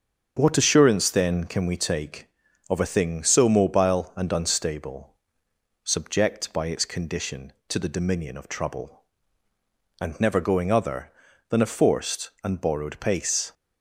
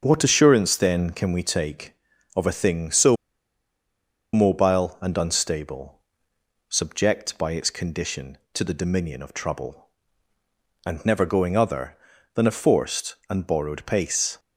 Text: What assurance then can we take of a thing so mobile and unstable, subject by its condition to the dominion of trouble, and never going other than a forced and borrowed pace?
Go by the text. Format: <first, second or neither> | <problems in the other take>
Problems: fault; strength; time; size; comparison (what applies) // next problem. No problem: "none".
first | starts louder than the rest; until 1.0 s; 7 dB; strong in the first // pauses between "so" and "mobile"; at 3.1 s; 1.1 s long